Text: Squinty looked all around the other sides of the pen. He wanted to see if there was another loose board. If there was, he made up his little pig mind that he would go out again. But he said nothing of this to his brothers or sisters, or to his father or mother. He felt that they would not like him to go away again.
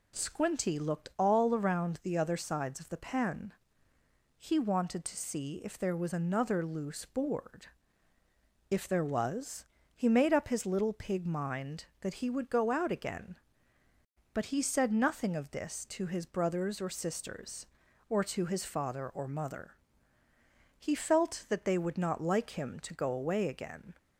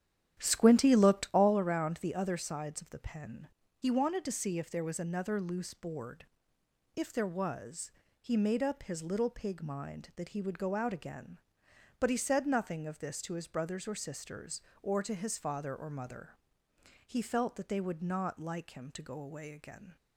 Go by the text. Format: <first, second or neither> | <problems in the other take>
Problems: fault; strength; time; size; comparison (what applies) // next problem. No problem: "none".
first | starts louder than the rest; strong; until 1.6 s; 10.5 dB